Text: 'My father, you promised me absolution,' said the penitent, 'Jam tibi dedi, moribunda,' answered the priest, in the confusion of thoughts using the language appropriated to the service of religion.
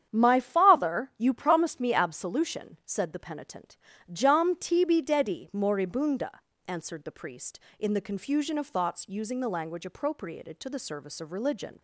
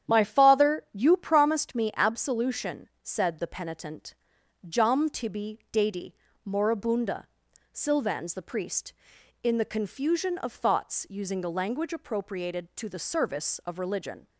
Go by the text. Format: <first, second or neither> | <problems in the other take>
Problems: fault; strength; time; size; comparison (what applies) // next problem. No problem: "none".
first | starts louder than the rest; strong; until 1.1 s; 9.5 dB; strong in the first // says "silvans" for "answered"; at 7.7 s